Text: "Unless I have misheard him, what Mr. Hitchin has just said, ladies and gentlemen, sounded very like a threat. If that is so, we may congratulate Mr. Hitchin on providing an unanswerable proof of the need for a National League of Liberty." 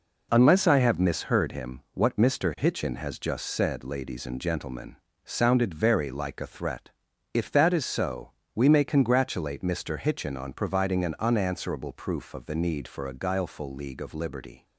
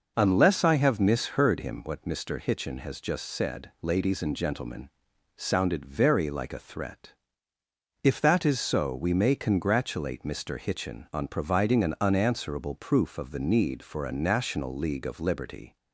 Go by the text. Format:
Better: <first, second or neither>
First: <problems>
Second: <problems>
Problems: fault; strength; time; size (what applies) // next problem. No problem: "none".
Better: second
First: says "Guileful" for "National"; at 13.1 s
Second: none